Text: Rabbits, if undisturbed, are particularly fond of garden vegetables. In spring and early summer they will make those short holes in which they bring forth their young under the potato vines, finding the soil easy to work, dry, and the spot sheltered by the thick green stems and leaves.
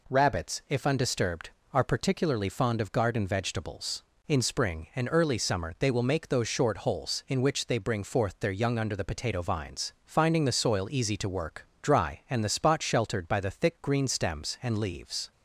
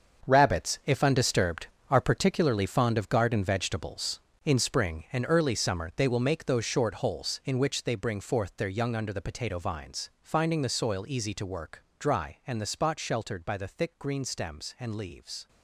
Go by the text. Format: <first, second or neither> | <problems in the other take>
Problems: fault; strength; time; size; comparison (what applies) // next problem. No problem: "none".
first | gets quieter; strong; throughout; 12.5 dB